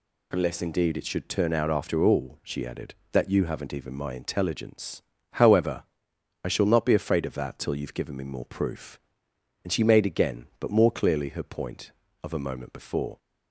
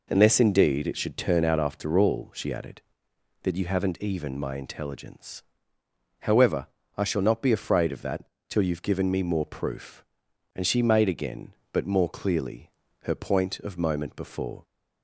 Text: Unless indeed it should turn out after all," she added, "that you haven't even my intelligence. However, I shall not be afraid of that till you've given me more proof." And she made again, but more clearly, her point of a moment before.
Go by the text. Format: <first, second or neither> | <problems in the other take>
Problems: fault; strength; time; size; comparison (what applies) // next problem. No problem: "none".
first | pauses between "that" and "till"; slight; at 8.2 s; 0.24 s long // skips "a"; at 13.7 s